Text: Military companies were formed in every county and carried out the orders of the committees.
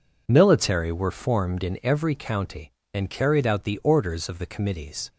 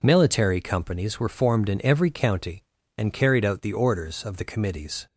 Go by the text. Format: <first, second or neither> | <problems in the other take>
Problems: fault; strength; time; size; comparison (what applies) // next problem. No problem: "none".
second | skips "companies"; at 0.9 s